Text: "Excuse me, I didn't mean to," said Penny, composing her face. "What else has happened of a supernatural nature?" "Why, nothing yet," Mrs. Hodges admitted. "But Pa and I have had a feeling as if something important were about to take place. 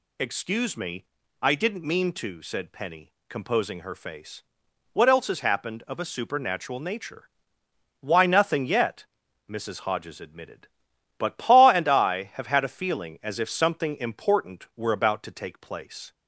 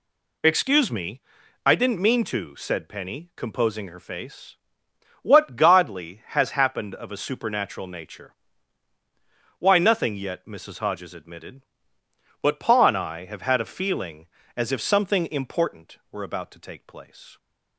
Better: first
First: none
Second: says "godly" for "else"; at 5.5 s

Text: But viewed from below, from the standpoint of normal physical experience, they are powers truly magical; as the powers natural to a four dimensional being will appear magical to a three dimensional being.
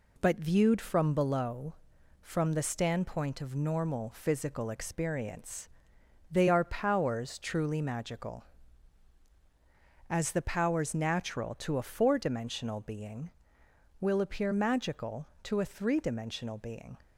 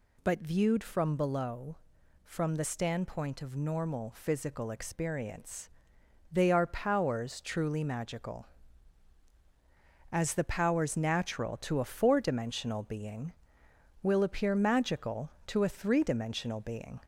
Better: first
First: none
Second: gets louder; slight; throughout; 2 dB

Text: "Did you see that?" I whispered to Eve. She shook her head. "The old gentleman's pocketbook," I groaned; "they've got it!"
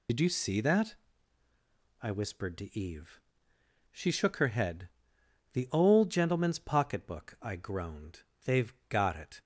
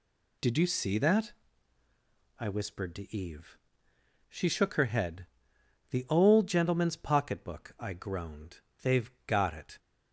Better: second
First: loses the start of "Did"; at 0.0 s; 70 ms // pauses between "they've" and "got"; slight; at 8.7 s; 0.16 s long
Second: pauses between "they've" and "got"; slight; at 9.1 s; 0.16 s long

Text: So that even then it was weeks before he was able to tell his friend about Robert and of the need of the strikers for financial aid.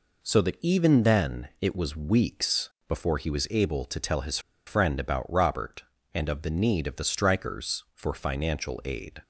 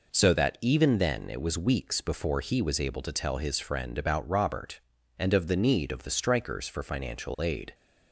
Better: second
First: pauses between "weeks" and "before"; slight; at 2.6 s; 0.20 s long // pauses between "his" and "friend"; slight; at 4.3 s; 0.28 s long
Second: none

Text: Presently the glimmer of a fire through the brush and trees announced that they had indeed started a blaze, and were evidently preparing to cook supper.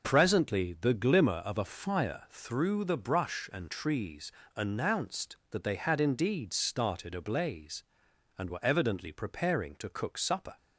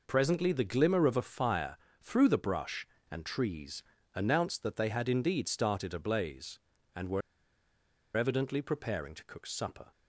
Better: first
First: pauses between "trees" and "announced"; slight; at 4.2 s; 0.26 s long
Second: pauses between "fire" and "through"; slight; at 1.7 s; 0.22 s long // pauses between "trees" and "announced"; slight; at 3.8 s; 0.32 s long // pauses between "were" and "evidently"; noticeable; at 7.2 s; 0.96 s long

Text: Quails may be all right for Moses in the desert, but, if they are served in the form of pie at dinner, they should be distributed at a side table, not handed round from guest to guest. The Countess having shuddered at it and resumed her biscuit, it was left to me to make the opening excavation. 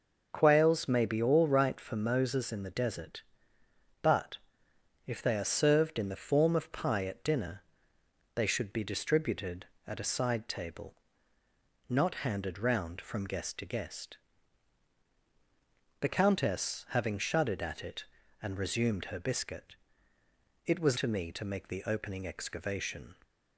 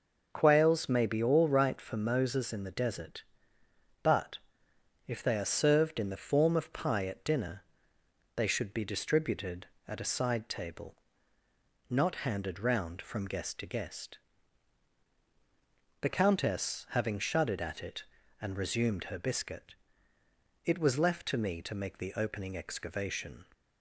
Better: second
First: skips "left"; at 20.9 s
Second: none

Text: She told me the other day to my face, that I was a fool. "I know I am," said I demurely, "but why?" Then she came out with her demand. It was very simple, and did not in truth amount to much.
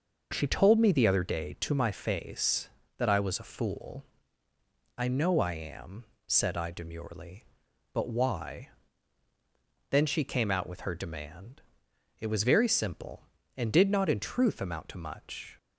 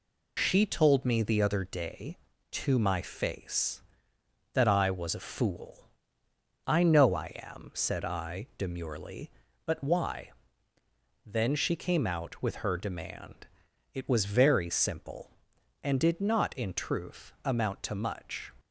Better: first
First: none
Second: loses the start of "She"; at 0.3 s; 55 ms

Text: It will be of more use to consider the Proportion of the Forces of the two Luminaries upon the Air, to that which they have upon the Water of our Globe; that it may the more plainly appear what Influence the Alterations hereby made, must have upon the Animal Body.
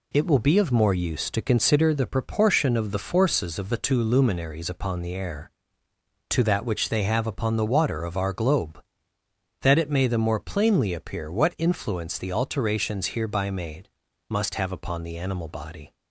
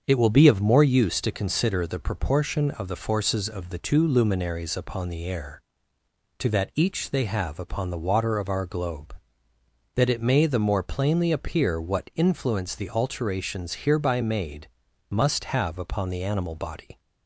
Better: first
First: none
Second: starts louder than the rest; until 1.0 s; 7 dB // says "each" for "which"; at 6.7 s

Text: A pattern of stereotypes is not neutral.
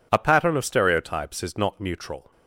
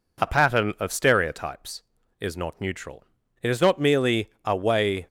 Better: first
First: none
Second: goes on to say "It is not merely a way"; from 3.4 s on; 1.6 s long

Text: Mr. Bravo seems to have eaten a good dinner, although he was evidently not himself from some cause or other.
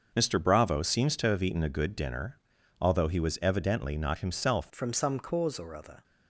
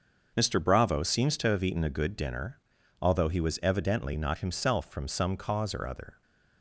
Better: second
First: starts louder than the rest; noticeable; until 1.1 s; 6 dB // changes voice at "from"; from 4.7 s on; 1.3 s long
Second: starts louder than the rest; until 1.3 s; 6.5 dB

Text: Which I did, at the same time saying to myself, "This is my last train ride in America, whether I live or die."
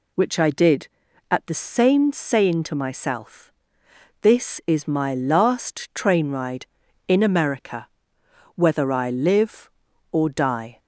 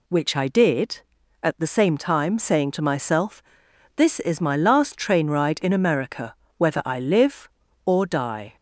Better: second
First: skips "time"; at 2.1 s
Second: none

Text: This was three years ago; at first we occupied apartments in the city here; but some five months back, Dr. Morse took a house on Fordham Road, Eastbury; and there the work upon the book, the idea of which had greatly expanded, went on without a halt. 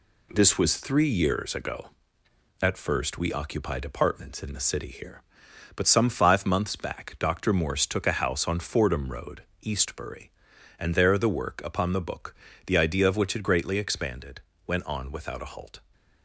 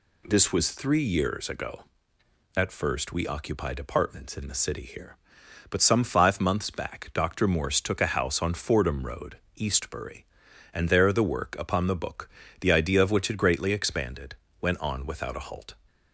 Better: second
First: gets quieter; noticeable; throughout; 4.5 dB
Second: none

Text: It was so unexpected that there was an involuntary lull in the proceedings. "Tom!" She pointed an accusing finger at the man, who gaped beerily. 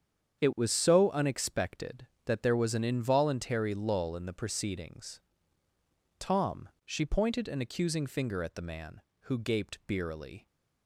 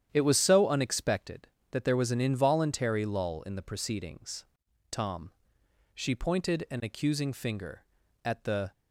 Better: first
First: starts louder than the rest; strong; until 1.4 s; 8 dB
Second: starts louder than the rest; strong; until 1.1 s; 10 dB // stops before "man who gaped beerily"; at 8.7 s

